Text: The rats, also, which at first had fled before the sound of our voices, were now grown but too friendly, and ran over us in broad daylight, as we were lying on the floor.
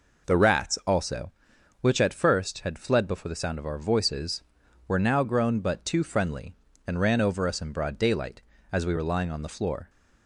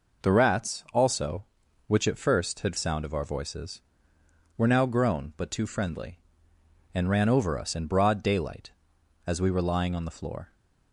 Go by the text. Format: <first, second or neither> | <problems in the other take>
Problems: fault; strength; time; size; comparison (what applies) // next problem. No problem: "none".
first | skips "fled before the"; at 2.7 s